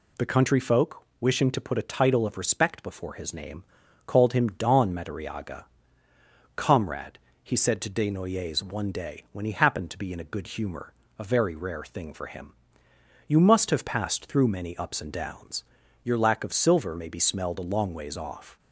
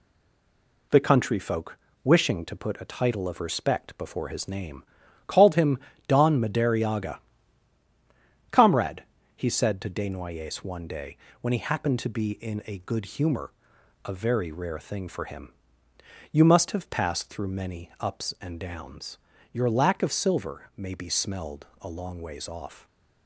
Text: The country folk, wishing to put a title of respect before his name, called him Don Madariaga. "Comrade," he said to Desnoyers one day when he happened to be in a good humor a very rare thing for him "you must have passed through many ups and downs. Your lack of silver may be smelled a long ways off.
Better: first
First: pauses between "humor" and "a"; slight; at 10.9 s; 0.26 s long // pauses between "him" and "you"; noticeable; at 12.5 s; 0.74 s long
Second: stays silent before the first word; slight; until 0.9 s; 0.9 s long // pauses between "him" and "Don"; slight; at 5.7 s; 0.28 s long // pauses between "day" and "when"; slight; at 11.1 s; 0.24 s long // pauses between "humor" and "a"; noticeable; at 13.5 s; 0.54 s long // pauses between "him" and "you"; noticeable; at 15.5 s; 0.78 s long

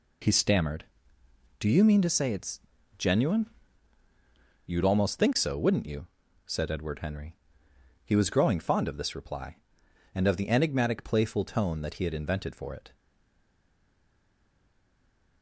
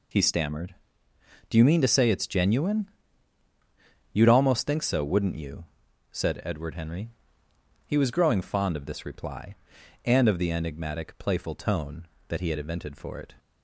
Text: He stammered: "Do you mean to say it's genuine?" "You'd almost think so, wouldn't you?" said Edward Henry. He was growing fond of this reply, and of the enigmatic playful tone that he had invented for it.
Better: second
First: pauses between "it's" and "genuine"; slight; at 2.6 s; 0.36 s long // stays silent after the last word; from 12.9 s on; 2.5 s long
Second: none

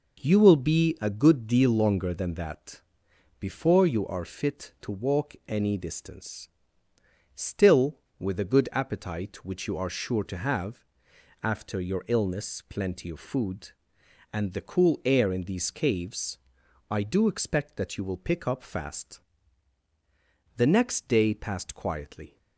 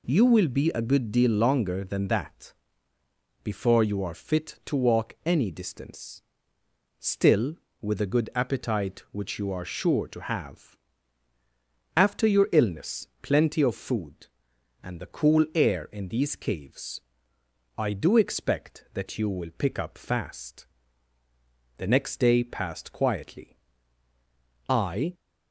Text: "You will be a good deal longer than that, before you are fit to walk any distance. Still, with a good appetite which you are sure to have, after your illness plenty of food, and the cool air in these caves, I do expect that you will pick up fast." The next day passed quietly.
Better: first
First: none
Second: pauses between "illness" and "plenty"; slight; at 13.0 s; 0.16 s long // goes on to say "I"; slight; from 24.6 s on; 0.46 s long

